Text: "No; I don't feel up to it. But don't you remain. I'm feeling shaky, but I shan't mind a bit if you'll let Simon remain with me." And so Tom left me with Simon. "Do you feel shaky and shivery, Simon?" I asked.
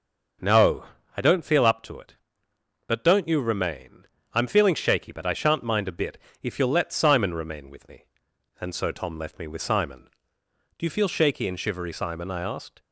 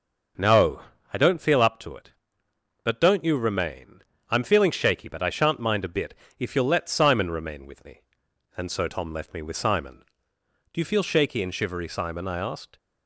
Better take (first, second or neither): neither